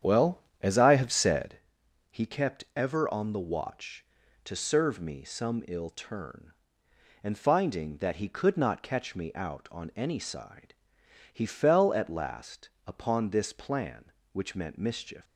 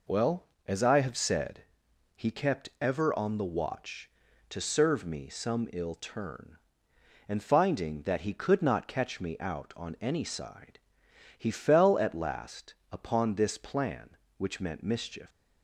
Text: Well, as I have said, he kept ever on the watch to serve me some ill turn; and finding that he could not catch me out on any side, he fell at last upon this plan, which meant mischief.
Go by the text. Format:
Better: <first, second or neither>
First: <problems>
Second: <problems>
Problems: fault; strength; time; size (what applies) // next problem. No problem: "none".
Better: second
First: starts louder than the rest; strong; until 1.6 s; 9 dB // pauses between "last" and "upon"; slight; at 12.6 s; 0.20 s long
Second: pauses between "last" and "upon"; slight; at 12.7 s; 0.20 s long